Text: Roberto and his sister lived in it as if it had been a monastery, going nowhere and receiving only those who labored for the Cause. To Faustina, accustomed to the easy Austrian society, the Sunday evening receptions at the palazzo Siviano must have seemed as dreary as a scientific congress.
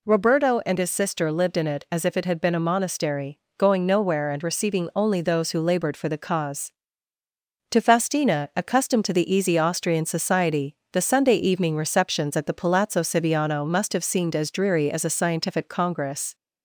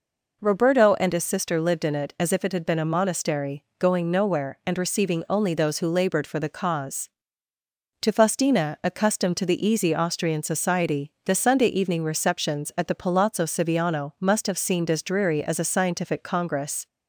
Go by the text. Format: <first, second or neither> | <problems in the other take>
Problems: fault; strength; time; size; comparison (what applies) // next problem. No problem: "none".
neither | none